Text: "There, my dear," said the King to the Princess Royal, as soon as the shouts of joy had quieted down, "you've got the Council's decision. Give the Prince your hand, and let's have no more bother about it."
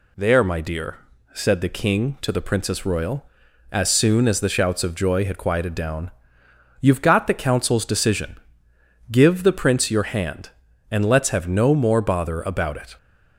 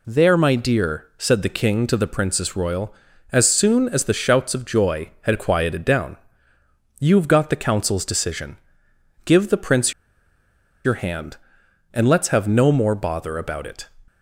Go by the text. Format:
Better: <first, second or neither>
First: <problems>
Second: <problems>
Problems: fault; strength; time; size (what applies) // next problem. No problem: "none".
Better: first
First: none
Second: pauses between "Prince" and "your"; noticeable; at 9.9 s; 0.91 s long